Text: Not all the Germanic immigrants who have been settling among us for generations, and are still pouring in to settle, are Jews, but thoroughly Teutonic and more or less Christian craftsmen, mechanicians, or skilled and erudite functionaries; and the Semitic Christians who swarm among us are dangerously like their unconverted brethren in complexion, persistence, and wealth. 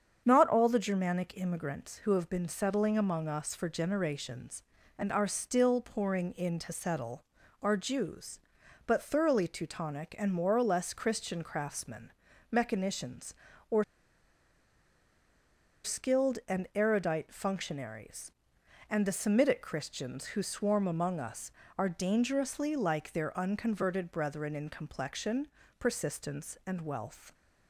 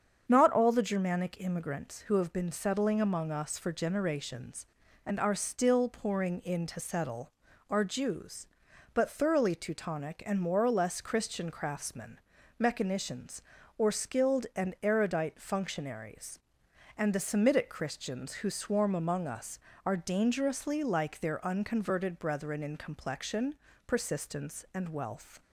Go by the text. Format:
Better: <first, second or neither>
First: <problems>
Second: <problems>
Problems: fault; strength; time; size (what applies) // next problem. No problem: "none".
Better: second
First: starts louder than the rest; strong; until 1.2 s; 7.5 dB // pauses between "or" and "skilled"; strong; at 13.8 s; 2.0 s long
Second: starts louder than the rest; strong; until 1.2 s; 7.5 dB